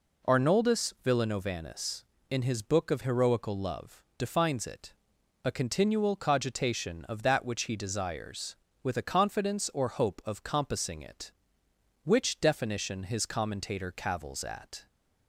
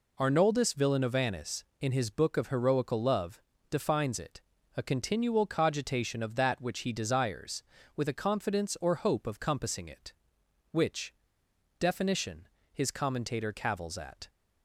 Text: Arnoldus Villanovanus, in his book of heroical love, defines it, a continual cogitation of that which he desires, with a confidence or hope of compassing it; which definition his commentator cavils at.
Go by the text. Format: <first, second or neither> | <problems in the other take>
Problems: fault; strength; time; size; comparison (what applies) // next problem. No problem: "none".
first | pauses between "which" and "definition"; noticeable; at 11.1 s; 0.64 s long // pauses between "definition" and "his"; slight; at 12.4 s; 0.26 s long